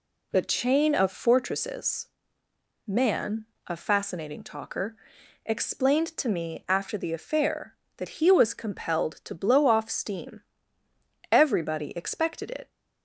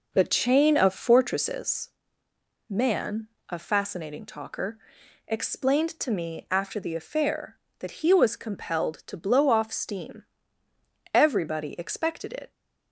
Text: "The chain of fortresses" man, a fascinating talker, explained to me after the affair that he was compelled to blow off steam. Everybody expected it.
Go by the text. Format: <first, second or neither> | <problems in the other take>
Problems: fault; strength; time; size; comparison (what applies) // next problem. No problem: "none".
first | starts louder than the rest; noticeable; until 1.8 s; 5 dB // pauses between "fortresses" and "man"; noticeable; at 1.8 s; 0.80 s long; noticeable in the first